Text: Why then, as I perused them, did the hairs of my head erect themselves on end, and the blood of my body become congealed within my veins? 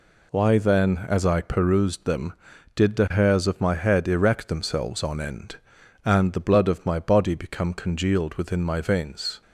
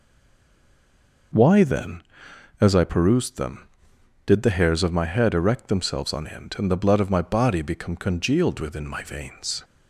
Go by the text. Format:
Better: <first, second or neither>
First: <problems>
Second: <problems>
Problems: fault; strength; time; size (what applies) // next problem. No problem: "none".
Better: first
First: none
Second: stays silent before the first word; noticeable; until 1.3 s; 1.3 s long